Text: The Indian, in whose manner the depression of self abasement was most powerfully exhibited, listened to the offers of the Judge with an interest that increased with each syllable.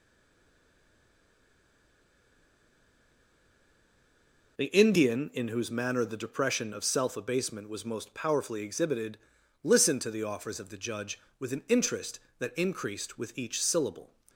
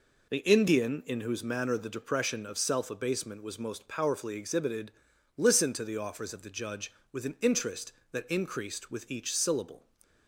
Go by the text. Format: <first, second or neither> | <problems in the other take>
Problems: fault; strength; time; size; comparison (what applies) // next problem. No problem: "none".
second | stays silent before the first word; strong; until 4.5 s; 4.5 s long